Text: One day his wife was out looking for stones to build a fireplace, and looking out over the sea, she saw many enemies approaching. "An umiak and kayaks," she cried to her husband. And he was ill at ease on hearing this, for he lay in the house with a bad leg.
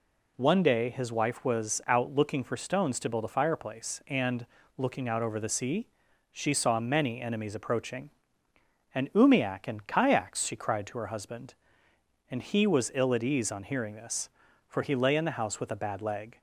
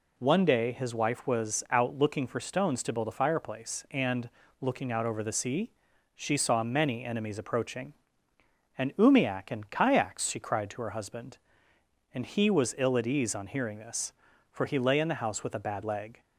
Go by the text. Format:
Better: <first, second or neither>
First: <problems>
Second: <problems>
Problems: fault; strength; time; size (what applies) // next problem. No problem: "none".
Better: neither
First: pauses between "and" and "looking"; slight; at 4.4 s; 0.32 s long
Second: pauses between "and" and "looking"; slight; at 4.3 s; 0.32 s long